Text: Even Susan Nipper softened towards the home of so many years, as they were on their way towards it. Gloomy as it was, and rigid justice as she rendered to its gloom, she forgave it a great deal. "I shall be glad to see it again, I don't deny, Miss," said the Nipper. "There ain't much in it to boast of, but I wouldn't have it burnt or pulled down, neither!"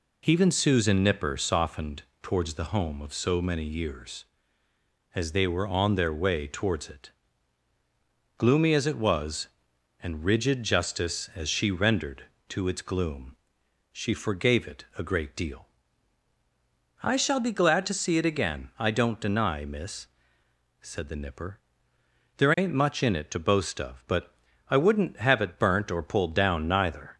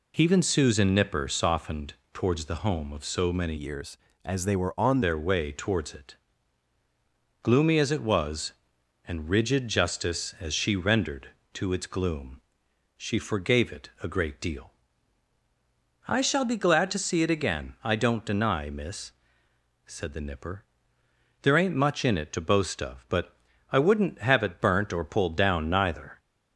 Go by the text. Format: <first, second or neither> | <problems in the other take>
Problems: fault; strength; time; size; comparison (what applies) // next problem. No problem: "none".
first | pauses between "softened" and "towards"; slight; at 1.9 s; 0.18 s long; slight in the first // changes voice from "years" to "on"; from 3.5 to 5.0 s; 1.5 s long // pauses between "but" and "I"; slight; at 23.3 s; 0.32 s long; slight in the first